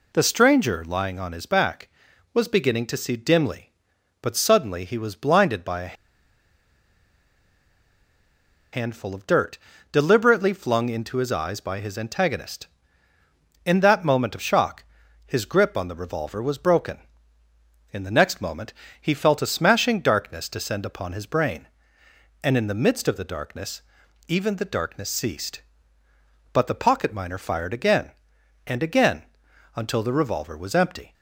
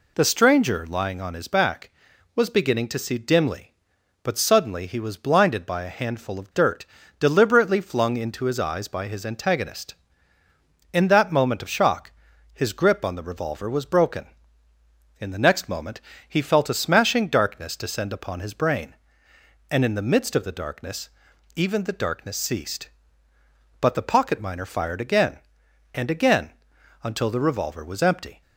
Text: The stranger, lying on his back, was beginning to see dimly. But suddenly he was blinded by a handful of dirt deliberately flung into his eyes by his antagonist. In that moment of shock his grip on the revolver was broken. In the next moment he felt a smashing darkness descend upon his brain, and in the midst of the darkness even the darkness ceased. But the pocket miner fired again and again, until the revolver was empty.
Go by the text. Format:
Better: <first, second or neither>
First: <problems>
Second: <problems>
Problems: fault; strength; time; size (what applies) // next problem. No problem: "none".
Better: second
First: pauses between "a" and "handful"; strong; at 5.9 s; 2.7 s long // pauses between "dirt" and "deliberately"; slight; at 9.5 s; 0.34 s long // pauses between "shock" and "his"; at 14.8 s; 0.42 s long // pauses between "moment" and "he"; slight; at 18.7 s; 0.30 s long // pauses between "darkness" and "even"; noticeable; at 23.8 s; 0.46 s long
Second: pauses between "dirt" and "deliberately"; slight; at 6.8 s; 0.34 s long // pauses between "shock" and "his"; at 12.1 s; 0.42 s long // pauses between "moment" and "he"; slight; at 15.9 s; 0.30 s long // pauses between "darkness" and "even"; noticeable; at 21.0 s; 0.46 s long